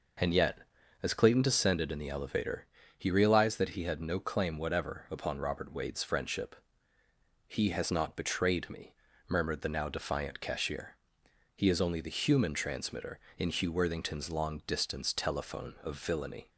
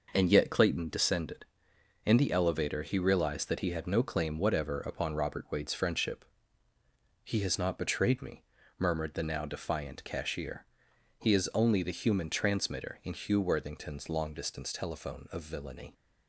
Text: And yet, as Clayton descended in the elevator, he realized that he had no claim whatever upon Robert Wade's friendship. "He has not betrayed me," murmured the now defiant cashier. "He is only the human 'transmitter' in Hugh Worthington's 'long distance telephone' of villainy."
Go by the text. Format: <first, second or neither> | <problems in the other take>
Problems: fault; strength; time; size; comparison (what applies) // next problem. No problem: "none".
first | skips "as"; at 0.4 s